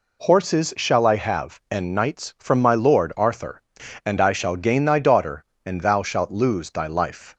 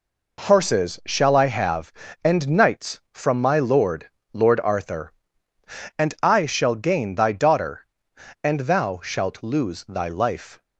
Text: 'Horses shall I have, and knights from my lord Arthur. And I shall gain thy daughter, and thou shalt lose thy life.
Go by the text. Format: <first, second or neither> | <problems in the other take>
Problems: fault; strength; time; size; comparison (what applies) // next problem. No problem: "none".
first | says "lord" twice; at 4.3 s